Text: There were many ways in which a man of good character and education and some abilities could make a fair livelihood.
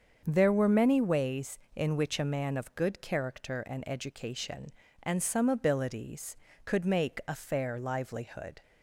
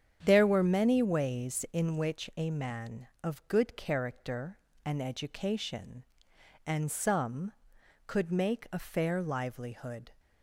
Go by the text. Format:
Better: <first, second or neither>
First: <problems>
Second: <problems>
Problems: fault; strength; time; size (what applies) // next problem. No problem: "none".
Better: first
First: starts louder than the rest; until 1.2 s; 7 dB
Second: starts louder than the rest; strong; until 1.2 s; 9 dB // skips "abilities"; at 7.7 s